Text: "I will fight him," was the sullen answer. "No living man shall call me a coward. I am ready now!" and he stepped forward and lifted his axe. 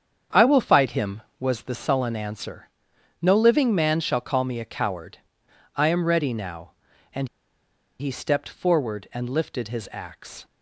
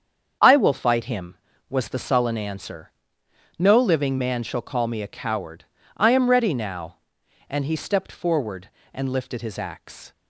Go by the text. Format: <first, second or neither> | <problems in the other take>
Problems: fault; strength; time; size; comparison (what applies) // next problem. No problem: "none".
second | starts louder than the rest; strong; until 1.5 s; 8 dB; strong in the second // pauses between "and" and "he"; noticeable; at 7.2 s; 0.72 s long